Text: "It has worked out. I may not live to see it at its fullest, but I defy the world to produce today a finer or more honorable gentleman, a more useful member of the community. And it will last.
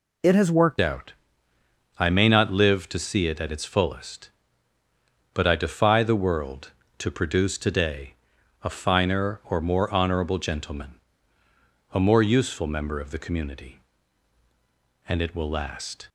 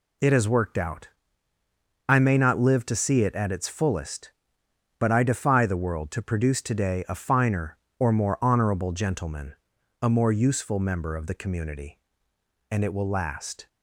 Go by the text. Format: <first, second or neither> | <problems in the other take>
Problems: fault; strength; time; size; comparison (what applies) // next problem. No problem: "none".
second | changes voice at "out"; from 0.8 s on; 15.2 s long // pauses between "today" and "a"; noticeable; at 8.1 s; 0.48 s long